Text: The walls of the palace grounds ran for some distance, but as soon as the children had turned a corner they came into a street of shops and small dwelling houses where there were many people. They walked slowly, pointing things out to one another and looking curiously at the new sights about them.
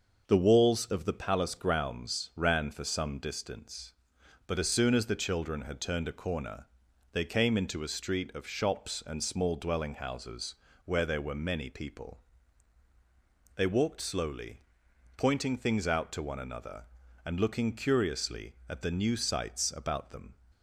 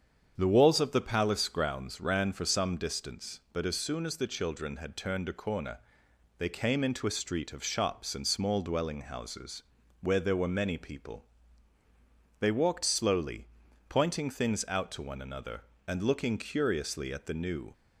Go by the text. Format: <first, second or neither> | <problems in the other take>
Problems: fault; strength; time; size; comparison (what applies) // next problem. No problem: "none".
first | starts louder than the rest; strong; until 1.3 s; 7.5 dB; noticeable in the first // pauses between "corner" and "they"; noticeable; at 5.7 s; 0.58 s long; also in the first // pauses between "houses" and "where"; at 9.6 s; 0.40 s long; slight in the first // stops before "sights about them"; at 17.7 s